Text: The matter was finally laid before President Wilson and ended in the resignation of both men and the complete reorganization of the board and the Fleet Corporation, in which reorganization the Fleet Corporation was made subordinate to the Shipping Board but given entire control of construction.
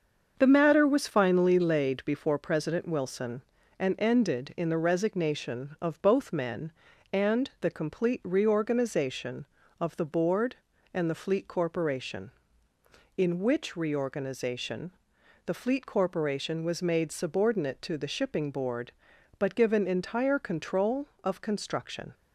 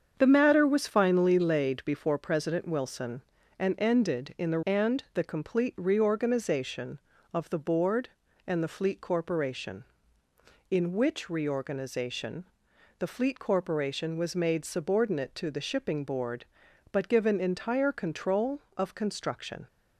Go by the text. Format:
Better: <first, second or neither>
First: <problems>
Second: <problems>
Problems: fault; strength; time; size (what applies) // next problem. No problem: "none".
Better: first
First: starts louder than the rest; until 1.3 s; 6.5 dB // pauses between "reorganization" and "the"; noticeable; at 14.8 s; 0.56 s long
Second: starts louder than the rest; strong; until 1.1 s; 7 dB // skips "resignation of both men"; at 4.6 s // pauses between "reorganization" and "the"; noticeable; at 12.4 s; 0.56 s long